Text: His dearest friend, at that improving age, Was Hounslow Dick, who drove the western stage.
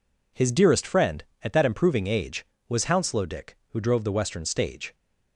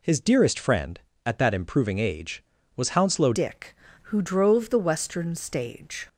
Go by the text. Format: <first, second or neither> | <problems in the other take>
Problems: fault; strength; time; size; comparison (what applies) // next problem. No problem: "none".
first | changes voice at "Dick"; from 3.3 s on; 2.7 s long